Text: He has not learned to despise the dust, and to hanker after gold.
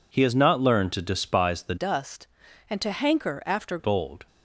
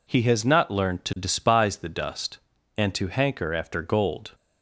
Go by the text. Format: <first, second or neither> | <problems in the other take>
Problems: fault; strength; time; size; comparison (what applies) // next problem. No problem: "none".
second | changes voice from "dust" to "after"; from 1.7 to 3.7 s; 2.0 s long